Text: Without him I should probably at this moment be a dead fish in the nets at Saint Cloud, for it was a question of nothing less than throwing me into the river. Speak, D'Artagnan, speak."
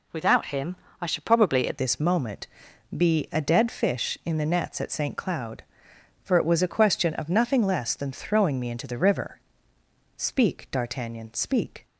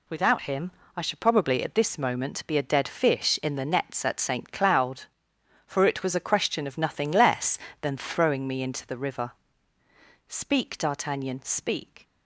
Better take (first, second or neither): second